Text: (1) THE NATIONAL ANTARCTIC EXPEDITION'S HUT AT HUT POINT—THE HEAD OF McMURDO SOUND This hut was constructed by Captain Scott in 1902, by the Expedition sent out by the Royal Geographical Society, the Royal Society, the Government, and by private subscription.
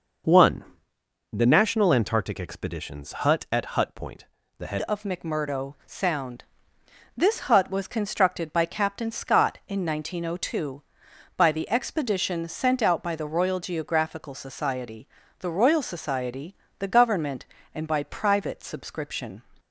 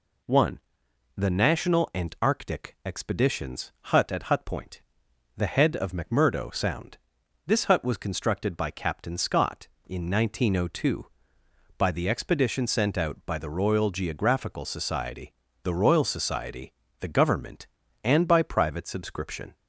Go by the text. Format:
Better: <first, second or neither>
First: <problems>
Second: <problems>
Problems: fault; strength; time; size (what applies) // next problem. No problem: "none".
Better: second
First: pauses between "EXPEDITION'S" and "HUT"; slight; at 3.1 s; 0.16 s long // changes voice at "OF"; from 4.8 s on; 14.6 s long // pauses between "SOUND" and "This"; noticeable; at 6.4 s; 0.70 s long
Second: pauses between "SOUND" and "This"; noticeable; at 6.9 s; 0.52 s long